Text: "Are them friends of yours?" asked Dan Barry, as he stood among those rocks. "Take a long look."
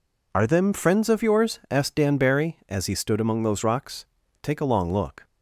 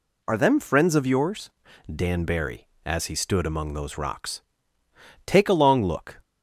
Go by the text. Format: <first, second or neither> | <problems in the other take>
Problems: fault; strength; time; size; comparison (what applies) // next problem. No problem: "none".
first | skips "asked"; at 1.7 s